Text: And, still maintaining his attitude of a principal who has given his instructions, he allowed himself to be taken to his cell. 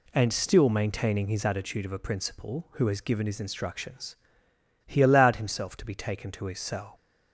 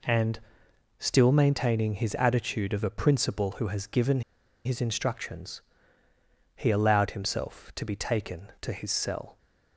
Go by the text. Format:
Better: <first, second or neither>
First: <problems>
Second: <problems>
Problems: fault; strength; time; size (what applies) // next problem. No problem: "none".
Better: first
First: none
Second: pauses between "given" and "his"; at 4.2 s; 0.43 s long